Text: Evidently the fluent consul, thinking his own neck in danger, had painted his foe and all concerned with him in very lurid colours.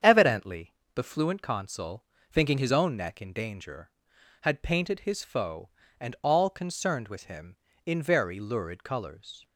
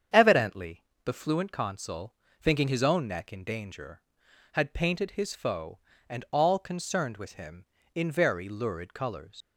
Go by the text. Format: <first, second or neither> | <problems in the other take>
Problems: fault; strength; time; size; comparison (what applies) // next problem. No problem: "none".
first | starts louder than the rest; strong; until 1.3 s; 8 dB; strong in the first // pauses between "Evidently" and "the"; slight; at 0.8 s; 0.22 s long; slight in the first // leaves "colours" unfinished; at 9.4 s; 150 ms